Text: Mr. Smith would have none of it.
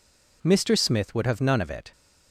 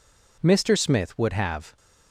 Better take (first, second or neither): first